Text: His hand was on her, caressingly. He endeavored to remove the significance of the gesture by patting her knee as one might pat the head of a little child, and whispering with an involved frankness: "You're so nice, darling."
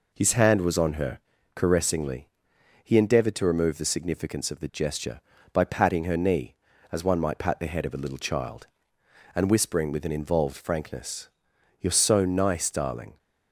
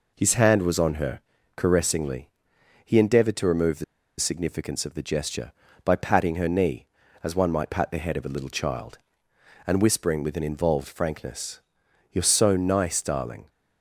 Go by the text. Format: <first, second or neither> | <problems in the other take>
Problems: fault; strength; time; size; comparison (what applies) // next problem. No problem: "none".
first | pauses between "the" and "significance"; slight; at 3.8 s; 0.35 s long